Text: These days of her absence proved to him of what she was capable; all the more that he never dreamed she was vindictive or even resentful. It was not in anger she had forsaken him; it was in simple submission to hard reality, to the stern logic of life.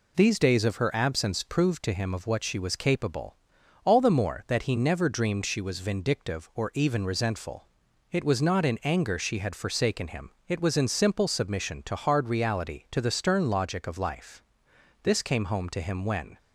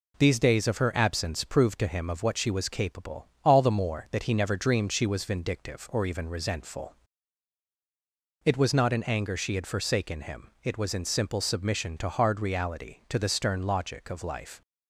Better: second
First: goes on to say "This came home to him when"; from 15.0 s on; 1.3 s long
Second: none

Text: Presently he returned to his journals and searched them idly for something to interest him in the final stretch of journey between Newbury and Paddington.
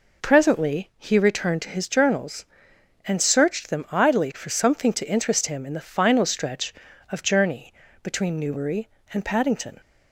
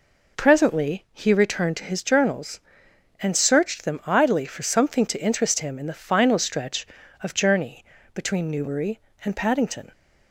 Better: neither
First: pauses between "journey" and "between"; slight; at 7.7 s; 0.32 s long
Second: pauses between "journey" and "between"; slight; at 7.8 s; 0.32 s long

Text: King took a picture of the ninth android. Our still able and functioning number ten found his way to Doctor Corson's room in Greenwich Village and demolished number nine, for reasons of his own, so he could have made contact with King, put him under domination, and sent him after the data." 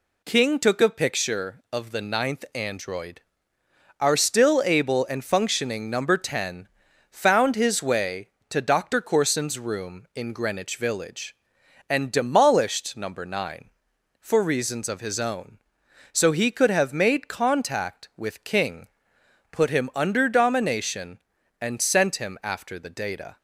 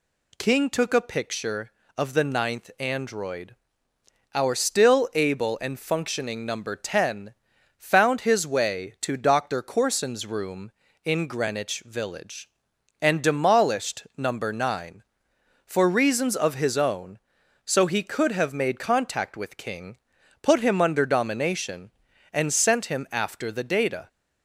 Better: neither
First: pauses between "ten" and "found"; at 6.6 s; 0.42 s long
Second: pauses between "ten" and "found"; at 7.3 s; 0.44 s long

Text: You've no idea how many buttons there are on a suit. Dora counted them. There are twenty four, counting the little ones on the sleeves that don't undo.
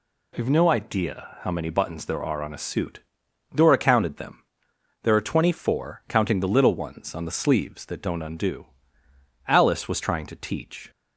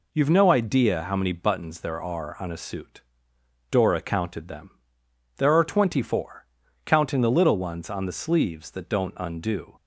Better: second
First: goes on to say "Alice was trying to teach"; from 9.4 s on; 1.4 s long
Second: none

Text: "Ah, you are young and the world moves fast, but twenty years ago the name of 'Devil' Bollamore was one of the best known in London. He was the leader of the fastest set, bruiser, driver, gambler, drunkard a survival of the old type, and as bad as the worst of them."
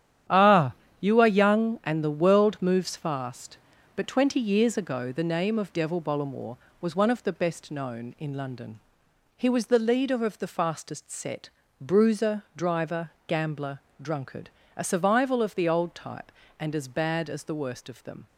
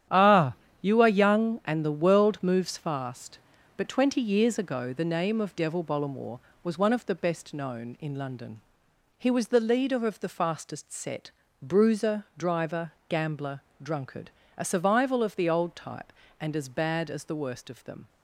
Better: neither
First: starts louder than the rest; strong; until 1.5 s; 10 dB // pauses between "drunkard" and "a"; slight; at 14.4 s; 0.26 s long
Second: starts louder than the rest; strong; until 1.4 s; 10.5 dB // pauses between "drunkard" and "a"; slight; at 14.3 s; 0.26 s long

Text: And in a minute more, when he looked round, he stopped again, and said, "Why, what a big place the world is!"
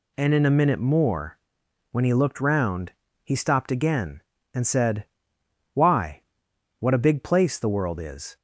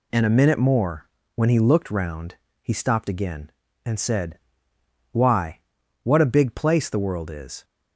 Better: first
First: none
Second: skips "in"; at 0.2 s

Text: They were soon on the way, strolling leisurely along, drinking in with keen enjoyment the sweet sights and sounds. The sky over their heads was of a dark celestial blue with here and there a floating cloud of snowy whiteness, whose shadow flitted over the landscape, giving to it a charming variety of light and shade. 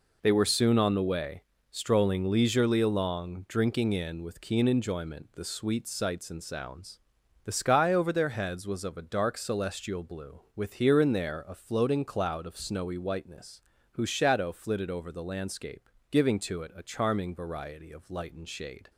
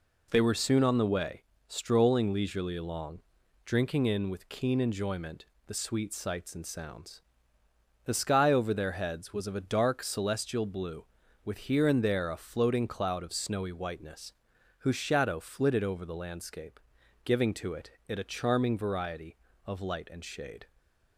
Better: first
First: none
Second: pauses between "enjoyment" and "the"; slight; at 5.4 s; 0.20 s long // says "it" twice; at 18.0 s

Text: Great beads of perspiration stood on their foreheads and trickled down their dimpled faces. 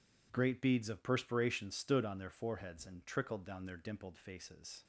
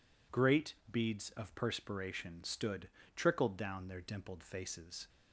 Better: first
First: none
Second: pauses between "Great" and "beads"; slight; at 0.7 s; 0.18 s long // skips "on their foreheads and"; at 3.0 s

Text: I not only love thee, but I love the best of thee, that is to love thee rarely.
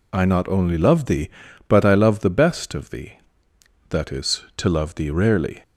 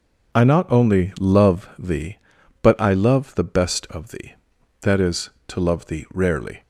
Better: neither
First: none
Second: none

